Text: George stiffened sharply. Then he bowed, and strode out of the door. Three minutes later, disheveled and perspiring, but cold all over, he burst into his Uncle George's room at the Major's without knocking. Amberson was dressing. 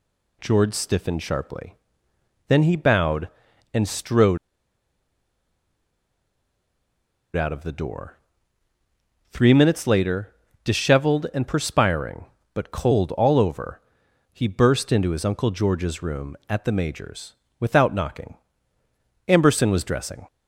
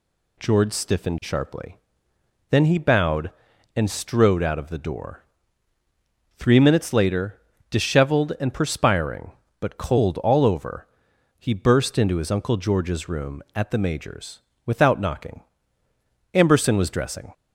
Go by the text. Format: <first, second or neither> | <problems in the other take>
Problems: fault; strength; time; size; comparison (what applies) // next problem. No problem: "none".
second | pauses between "strode" and "out"; strong; at 4.3 s; 2.9 s long // pauses between "Major's" and "without"; slight; at 17.3 s; 0.24 s long; slight in the second